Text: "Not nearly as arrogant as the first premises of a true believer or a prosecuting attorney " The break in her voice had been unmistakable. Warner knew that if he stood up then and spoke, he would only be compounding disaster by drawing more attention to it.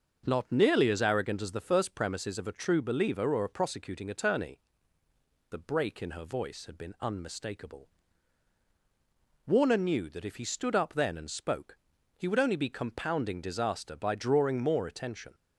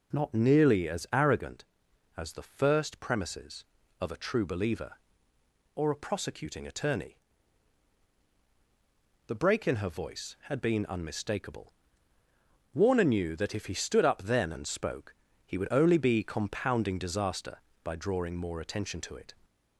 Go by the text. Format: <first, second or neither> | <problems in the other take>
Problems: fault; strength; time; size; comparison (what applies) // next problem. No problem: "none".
second | starts louder than the rest; until 1.2 s; 6.5 dB; also in the second // stops before "to it"; at 15.3 s